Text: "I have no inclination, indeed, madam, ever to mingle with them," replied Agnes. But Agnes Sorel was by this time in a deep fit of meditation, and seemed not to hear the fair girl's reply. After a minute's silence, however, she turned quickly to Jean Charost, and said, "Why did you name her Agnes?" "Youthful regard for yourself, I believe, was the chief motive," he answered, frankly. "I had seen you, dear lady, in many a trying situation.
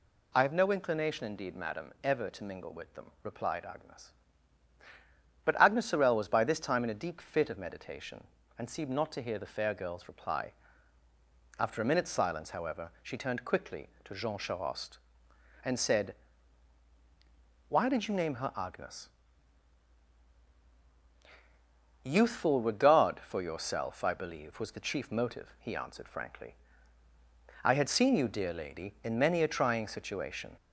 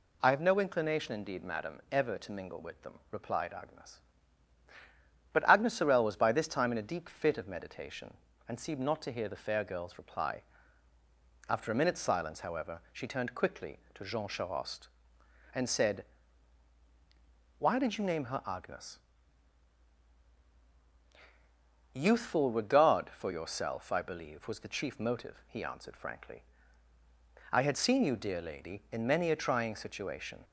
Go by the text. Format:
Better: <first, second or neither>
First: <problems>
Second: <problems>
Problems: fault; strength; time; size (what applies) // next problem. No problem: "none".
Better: second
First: gets louder; slight; throughout; 2.5 dB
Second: none